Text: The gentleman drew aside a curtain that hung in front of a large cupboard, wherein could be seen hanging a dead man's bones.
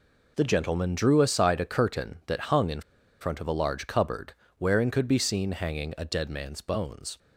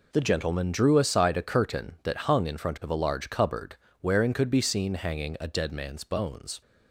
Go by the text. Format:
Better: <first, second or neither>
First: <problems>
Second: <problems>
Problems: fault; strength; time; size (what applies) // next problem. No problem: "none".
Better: second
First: pauses between "in" and "front"; at 2.8 s; 0.40 s long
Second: none